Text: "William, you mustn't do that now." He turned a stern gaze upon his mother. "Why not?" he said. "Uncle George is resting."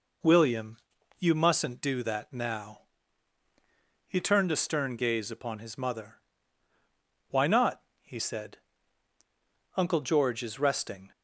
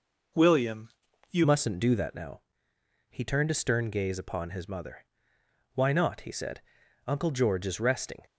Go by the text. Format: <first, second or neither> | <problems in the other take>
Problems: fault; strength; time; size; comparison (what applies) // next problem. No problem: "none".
first | changes voice at "mustn't"; from 1.4 s on; 6.8 s long